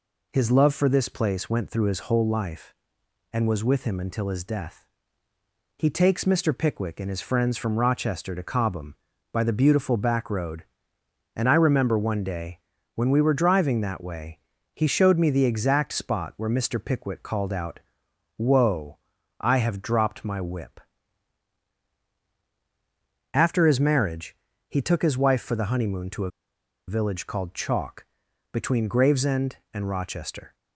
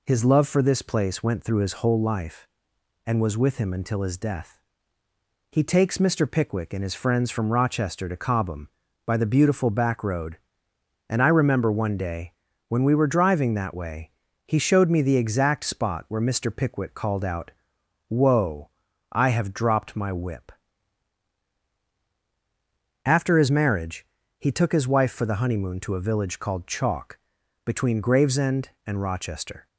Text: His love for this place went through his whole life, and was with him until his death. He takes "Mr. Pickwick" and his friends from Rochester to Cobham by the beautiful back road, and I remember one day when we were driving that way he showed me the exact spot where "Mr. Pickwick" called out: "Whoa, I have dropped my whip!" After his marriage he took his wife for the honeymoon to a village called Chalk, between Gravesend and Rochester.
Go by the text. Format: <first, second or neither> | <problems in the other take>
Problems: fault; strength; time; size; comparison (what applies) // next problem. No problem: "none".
second | pauses between "day" and "when"; slight; at 12.5 s; 0.36 s long; slight in the second // pauses between "way" and "he"; slight; at 14.3 s; 0.34 s long; slight in the second // pauses between "marriage" and "he"; slight; at 24.3 s; 0.34 s long; slight in the second // pauses between "a" and "village"; noticeable; at 26.3 s; 0.57 s long